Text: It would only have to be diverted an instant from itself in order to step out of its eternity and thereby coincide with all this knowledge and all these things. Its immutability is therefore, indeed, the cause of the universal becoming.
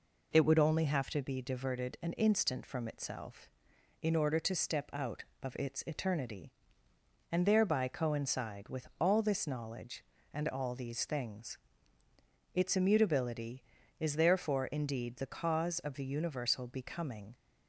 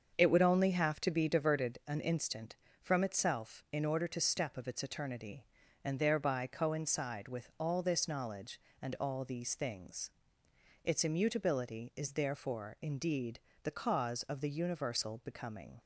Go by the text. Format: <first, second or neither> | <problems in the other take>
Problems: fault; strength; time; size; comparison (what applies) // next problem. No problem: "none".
first | starts louder than the rest; until 1.1 s; 7 dB // skips "out"; at 4.5 s